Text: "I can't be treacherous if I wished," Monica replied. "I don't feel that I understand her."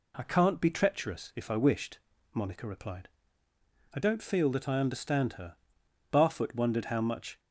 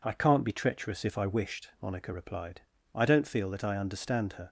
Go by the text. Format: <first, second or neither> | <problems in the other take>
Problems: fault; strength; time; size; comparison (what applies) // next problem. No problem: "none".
second | goes on to say "Barfoot wondered how much"; noticeable; from 6.1 s on; 1.2 s long